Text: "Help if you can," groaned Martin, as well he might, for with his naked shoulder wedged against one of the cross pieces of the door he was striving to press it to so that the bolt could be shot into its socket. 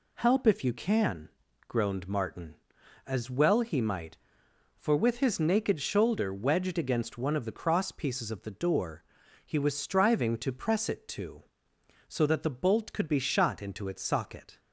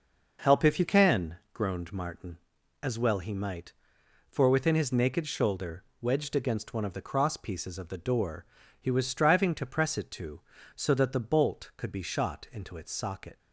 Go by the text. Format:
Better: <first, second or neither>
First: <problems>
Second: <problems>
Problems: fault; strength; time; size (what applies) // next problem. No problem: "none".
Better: first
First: pauses between "door" and "he"; at 9.0 s; 0.42 s long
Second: says "within" for "with"; at 4.4 s // pauses between "shoulder" and "wedged"; slight; at 5.8 s; 0.16 s long // pauses between "door" and "he"; slight; at 8.4 s; 0.34 s long